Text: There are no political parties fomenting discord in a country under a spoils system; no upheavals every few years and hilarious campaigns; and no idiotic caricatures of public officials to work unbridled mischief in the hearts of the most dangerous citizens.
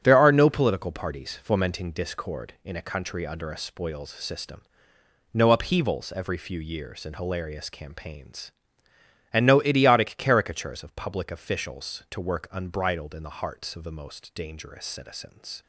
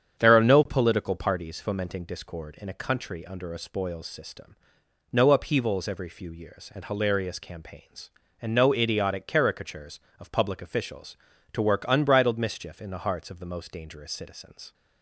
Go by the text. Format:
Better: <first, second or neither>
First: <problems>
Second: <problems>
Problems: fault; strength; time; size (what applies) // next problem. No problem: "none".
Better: second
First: starts louder than the rest; strong; until 1.0 s; 8 dB // skips "mischief"; at 13.1 s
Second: starts louder than the rest; strong; until 1.2 s; 8 dB